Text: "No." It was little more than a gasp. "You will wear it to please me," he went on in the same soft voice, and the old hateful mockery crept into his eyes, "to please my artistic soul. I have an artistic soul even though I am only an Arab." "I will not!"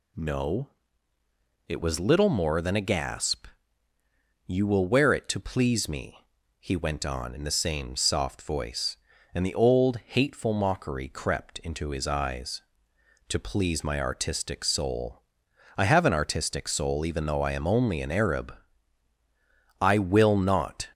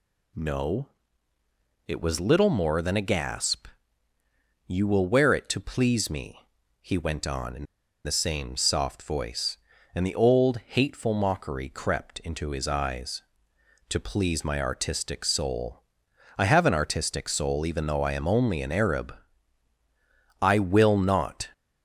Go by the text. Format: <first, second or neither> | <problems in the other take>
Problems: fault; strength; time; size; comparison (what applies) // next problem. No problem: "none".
first | pauses between "in" and "the"; at 7.6 s; 0.39 s long